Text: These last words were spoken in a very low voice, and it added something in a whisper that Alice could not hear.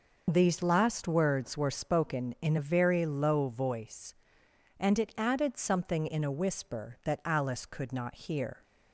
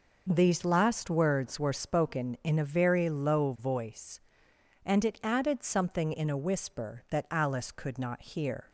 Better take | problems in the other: second | loses the start of "These"; at 0.2 s; 35 ms

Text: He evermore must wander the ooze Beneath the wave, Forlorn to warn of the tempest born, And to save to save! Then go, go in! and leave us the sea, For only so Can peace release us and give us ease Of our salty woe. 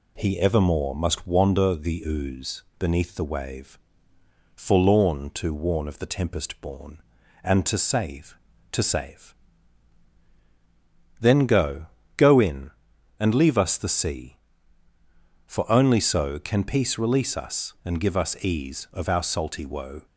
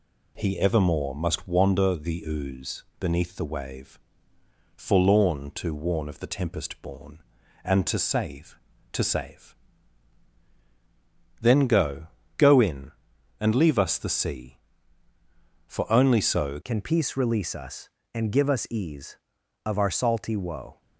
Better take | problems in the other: first | changes voice at "Can"; from 16.6 s on; 4.2 s long

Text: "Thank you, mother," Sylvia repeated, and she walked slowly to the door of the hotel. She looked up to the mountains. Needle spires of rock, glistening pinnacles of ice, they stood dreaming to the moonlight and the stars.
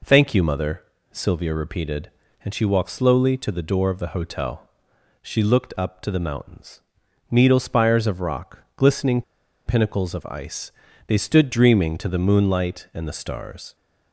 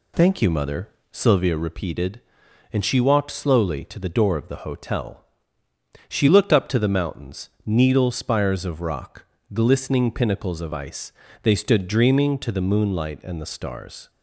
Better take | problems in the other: second | pauses between "glistening" and "pinnacles"; at 9.2 s; 0.44 s long

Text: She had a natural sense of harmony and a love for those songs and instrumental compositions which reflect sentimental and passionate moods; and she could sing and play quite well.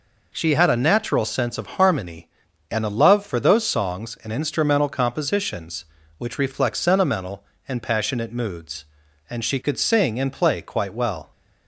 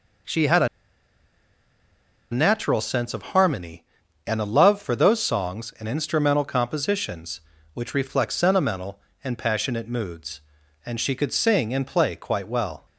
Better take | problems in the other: first | pauses between "a" and "natural"; strong; at 0.6 s; 1.6 s long

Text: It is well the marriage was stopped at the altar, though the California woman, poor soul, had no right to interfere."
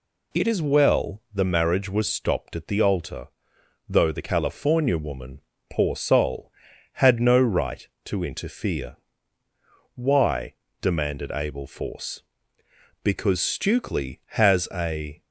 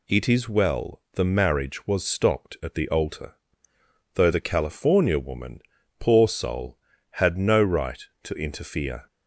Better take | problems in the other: second | goes on to say "Why demanded Abel Force Because Stukely has a"; strong; from 9.9 s on; 5.2 s long

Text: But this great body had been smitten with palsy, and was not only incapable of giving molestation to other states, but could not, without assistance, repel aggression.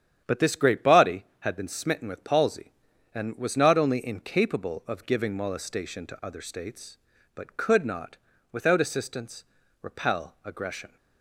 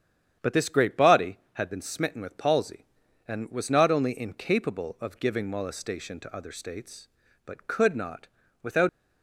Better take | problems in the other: first | starts louder than the rest; strong; until 1.5 s; 9 dB; strong in the first // stops before "assistance repel aggression"; at 8.8 s

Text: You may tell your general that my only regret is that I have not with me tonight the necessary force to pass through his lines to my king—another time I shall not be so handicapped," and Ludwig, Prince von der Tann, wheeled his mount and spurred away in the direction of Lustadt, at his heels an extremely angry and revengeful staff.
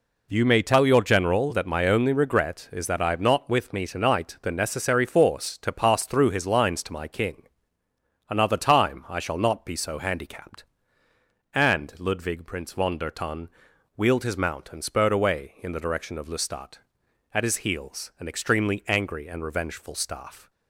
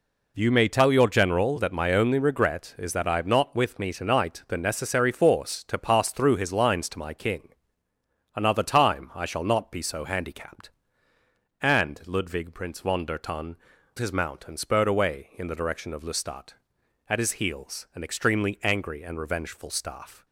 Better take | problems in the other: first | skips "wheeled"; at 13.7 s

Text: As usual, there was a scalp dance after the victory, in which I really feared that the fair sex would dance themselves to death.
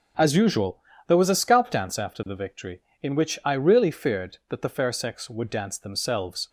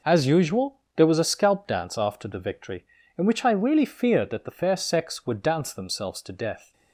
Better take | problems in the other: second | stops before "to death"; at 6.4 s

